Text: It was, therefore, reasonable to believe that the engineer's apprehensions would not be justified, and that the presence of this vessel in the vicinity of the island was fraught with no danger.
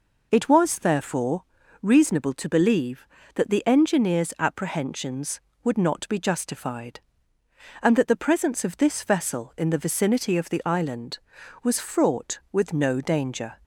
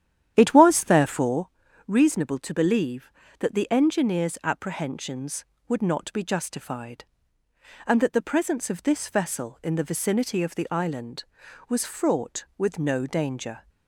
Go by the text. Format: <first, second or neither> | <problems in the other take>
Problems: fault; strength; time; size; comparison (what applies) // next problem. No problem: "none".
first | starts louder than the rest; strong; until 1.5 s; 10.5 dB